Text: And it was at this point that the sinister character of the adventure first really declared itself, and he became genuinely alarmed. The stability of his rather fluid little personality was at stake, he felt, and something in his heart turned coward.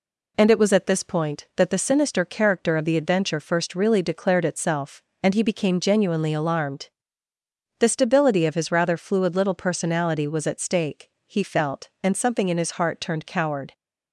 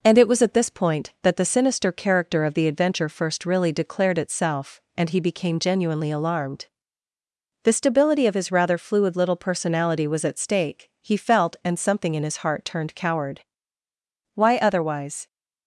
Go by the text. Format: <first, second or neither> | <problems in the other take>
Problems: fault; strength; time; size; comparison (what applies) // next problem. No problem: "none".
first | goes on to say "Why otherwise"; noticeable; from 14.3 s on; 0.92 s long